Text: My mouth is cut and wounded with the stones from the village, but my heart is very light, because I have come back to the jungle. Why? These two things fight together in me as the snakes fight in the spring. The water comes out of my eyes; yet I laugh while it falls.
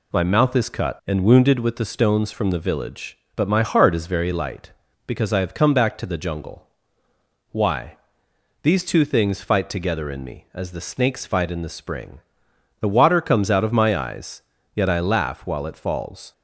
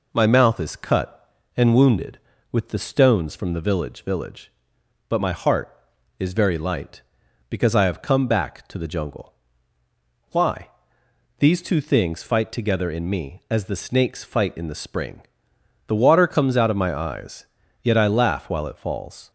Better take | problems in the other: first | says "village" twice; at 4.0 s

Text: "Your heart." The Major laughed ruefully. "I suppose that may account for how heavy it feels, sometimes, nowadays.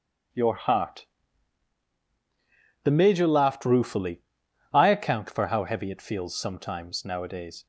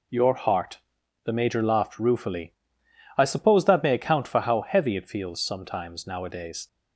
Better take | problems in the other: second | starts louder than the rest; strong; until 3.1 s; 9.5 dB // skips "suppose that may"; at 4.8 s

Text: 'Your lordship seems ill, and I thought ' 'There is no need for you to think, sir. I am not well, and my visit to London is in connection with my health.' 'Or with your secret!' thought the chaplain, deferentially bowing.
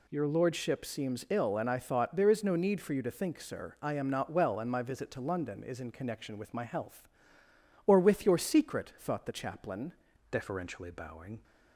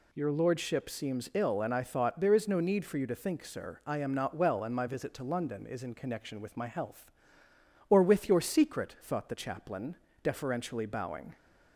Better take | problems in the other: second | changes voice at "deferentially"; from 10.2 s on; 1.2 s long

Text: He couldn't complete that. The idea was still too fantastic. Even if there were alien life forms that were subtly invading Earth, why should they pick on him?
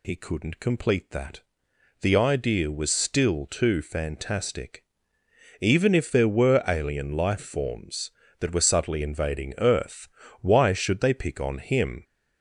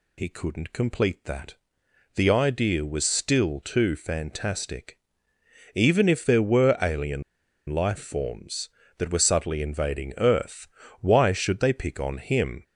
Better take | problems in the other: first | pauses between "alien" and "life"; noticeable; at 7.2 s; 0.46 s long

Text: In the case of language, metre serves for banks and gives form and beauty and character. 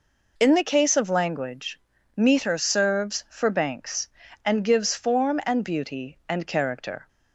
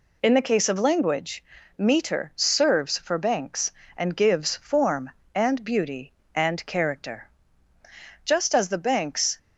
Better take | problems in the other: first | goes on to say "Just as the banks"; noticeable; from 8.2 s on; 1.1 s long

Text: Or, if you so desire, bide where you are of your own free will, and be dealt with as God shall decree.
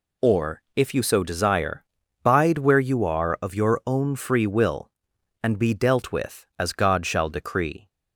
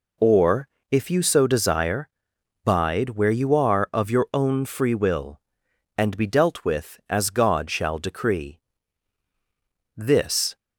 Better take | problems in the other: first | goes on to say "This"; noticeable; from 9.9 s on; 0.62 s long

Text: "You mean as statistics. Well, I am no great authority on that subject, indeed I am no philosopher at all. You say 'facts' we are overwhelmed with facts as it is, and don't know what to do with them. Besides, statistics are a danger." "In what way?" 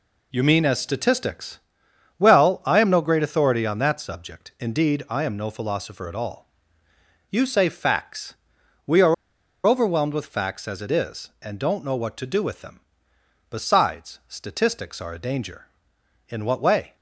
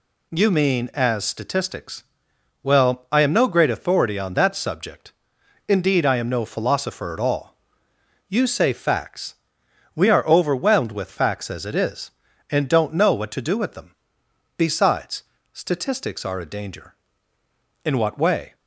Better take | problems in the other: second | pauses between "facts" and "we"; noticeable; at 8.3 s; 0.50 s long; noticeable in the second // pauses between "are" and "overwhelmed"; noticeable; at 9.1 s; 0.52 s long

